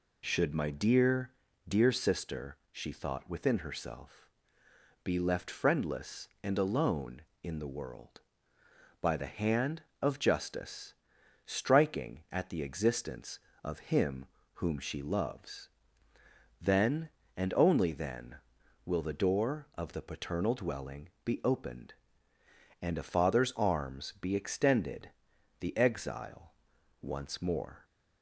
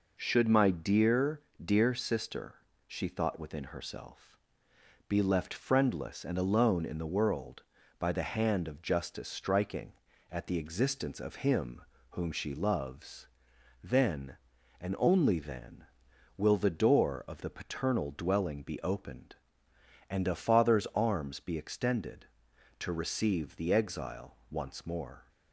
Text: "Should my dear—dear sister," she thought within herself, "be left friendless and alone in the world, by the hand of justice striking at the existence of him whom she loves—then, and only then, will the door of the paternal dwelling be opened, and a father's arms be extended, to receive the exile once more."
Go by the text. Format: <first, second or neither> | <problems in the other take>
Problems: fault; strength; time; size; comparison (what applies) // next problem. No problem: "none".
second | pauses between "justice" and "striking"; noticeable; at 10.9 s; 0.50 s long // pauses between "him" and "whom"; slight; at 14.2 s; 0.30 s long; slight in the second // pauses between "dwelling" and "be"; slight; at 21.1 s; 0.16 s long // skips "to receive"; at 25.3 s // pauses between "exile" and "once"; noticeable; at 26.5 s; 0.48 s long